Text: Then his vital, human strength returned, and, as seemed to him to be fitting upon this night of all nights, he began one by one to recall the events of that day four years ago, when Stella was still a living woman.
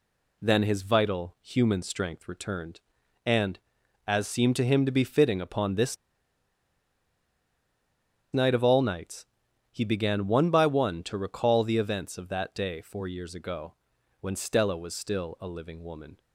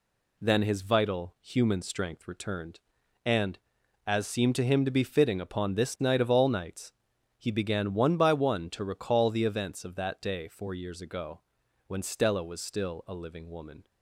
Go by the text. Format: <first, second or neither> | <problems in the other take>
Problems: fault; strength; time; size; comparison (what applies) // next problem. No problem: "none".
second | pauses between "this" and "night"; strong; at 5.9 s; 2.3 s long